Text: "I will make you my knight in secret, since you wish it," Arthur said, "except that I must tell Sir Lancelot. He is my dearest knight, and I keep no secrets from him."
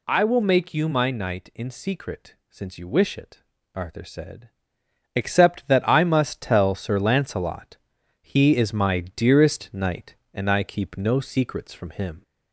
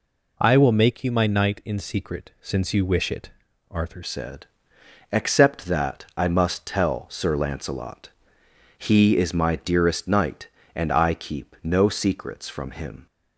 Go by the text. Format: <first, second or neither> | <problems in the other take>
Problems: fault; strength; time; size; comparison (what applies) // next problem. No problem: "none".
first | changes voice at "said"; from 4.0 s on; 9.0 s long